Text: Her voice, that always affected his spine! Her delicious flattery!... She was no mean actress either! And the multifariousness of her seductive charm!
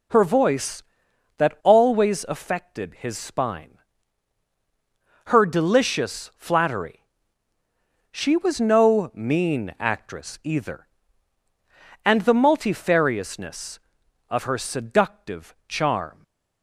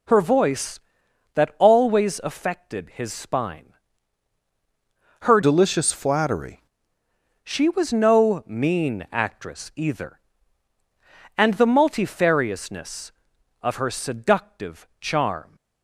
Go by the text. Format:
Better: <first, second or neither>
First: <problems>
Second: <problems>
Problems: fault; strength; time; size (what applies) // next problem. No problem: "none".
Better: first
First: none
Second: changes voice from "delicious" to "flattery"; from 5.4 to 6.6 s; 1.2 s long